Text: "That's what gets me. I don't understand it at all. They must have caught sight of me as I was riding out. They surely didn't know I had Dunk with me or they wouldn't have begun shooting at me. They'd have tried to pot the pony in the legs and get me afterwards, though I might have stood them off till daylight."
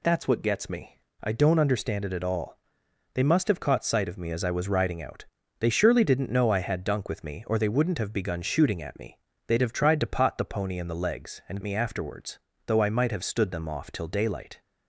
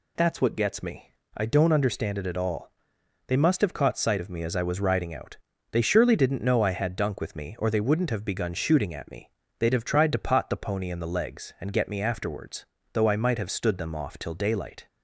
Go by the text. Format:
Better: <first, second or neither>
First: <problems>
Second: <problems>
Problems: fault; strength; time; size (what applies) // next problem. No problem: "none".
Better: second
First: skips "get"; at 11.6 s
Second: none